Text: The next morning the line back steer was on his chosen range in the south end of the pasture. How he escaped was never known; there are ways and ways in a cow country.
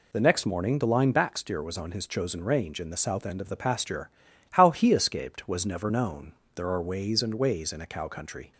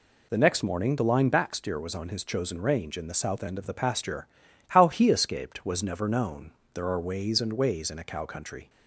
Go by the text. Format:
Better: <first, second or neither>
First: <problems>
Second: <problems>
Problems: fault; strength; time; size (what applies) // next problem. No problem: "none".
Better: neither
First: none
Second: none